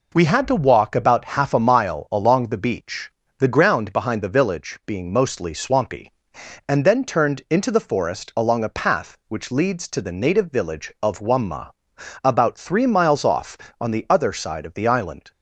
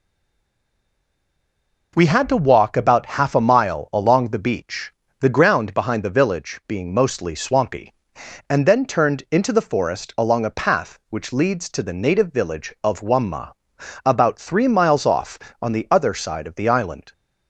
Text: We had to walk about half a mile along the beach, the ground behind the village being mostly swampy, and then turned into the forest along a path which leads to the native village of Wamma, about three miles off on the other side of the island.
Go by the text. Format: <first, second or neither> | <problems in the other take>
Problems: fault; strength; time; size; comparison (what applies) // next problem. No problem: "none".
first | stays silent before the first word; noticeable; until 1.9 s; 1.9 s long